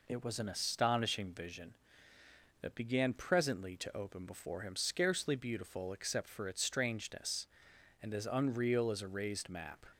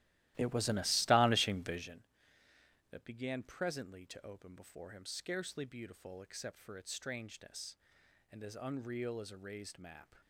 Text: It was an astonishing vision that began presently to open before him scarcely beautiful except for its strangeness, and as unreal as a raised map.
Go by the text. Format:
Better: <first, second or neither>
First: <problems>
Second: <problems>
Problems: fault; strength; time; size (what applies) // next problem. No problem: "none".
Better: first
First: none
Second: starts louder than the rest; strong; until 2.0 s; 15.5 dB